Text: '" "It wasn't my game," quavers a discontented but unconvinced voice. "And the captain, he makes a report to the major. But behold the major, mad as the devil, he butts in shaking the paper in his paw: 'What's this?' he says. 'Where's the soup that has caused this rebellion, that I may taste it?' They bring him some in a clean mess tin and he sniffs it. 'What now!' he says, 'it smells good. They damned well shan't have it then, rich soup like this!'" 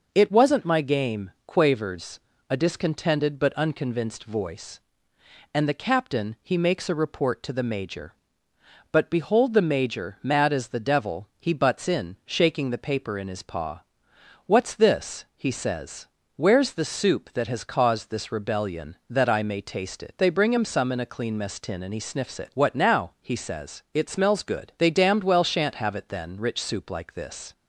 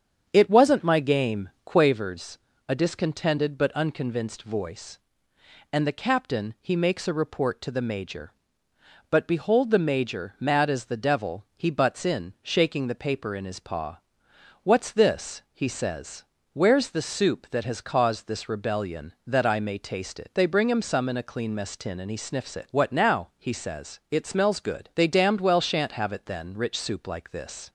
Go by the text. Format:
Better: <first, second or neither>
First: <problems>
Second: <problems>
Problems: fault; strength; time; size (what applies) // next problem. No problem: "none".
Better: first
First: pauses between "quavers" and "a"; slight; at 2.1 s; 0.30 s long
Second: starts louder than the rest; strong; until 2.1 s; 8 dB // pauses between "quavers" and "a"; slight; at 2.3 s; 0.30 s long